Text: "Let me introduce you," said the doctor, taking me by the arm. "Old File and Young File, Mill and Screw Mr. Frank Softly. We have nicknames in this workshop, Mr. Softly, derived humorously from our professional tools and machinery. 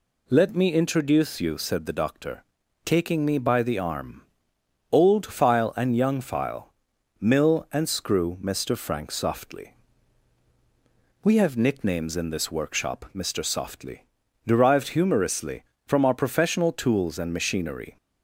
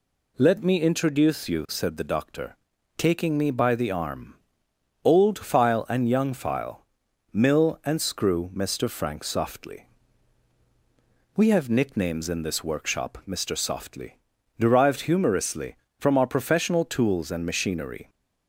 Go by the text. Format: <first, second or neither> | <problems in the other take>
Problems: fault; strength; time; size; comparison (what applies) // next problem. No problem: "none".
neither | none